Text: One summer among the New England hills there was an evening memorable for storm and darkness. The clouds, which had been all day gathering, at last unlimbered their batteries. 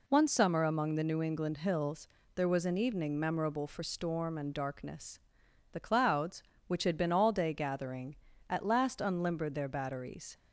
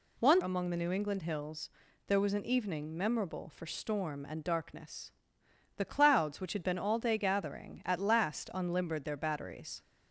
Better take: first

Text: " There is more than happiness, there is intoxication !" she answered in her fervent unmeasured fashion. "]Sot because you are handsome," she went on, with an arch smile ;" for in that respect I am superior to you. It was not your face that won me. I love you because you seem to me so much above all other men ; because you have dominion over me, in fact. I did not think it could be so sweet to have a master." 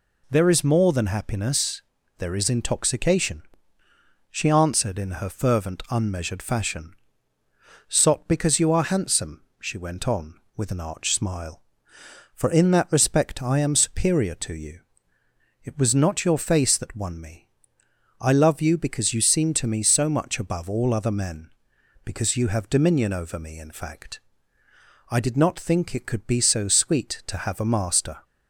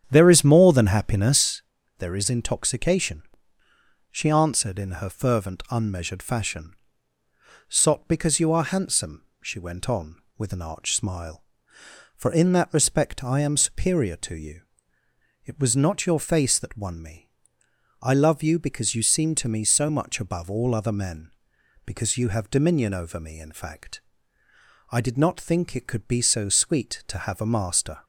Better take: first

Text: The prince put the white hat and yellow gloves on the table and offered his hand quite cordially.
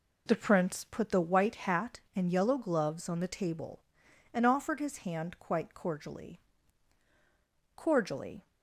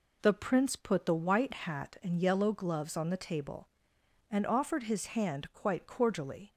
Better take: second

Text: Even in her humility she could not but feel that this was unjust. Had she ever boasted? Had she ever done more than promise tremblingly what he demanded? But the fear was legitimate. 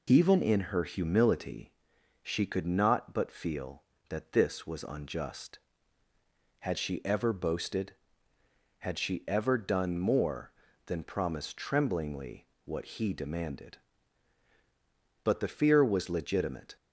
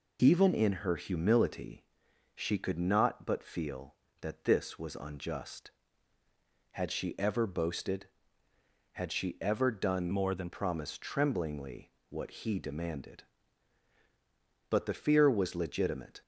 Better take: first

